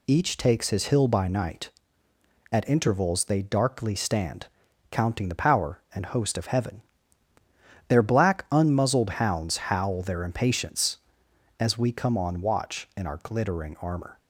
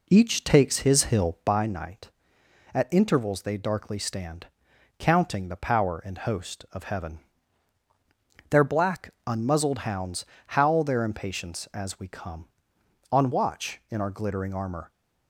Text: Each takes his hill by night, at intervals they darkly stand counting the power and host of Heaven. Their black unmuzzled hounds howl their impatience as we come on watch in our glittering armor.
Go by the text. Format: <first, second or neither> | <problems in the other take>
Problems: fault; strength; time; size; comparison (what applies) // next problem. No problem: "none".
first | starts louder than the rest; slight; until 1.6 s; 3.5 dB // pauses between "stand" and "counting"; noticeable; at 4.4 s; 0.52 s long; also in the first // pauses between "hounds" and "howl"; slight; at 10.2 s; 0.22 s long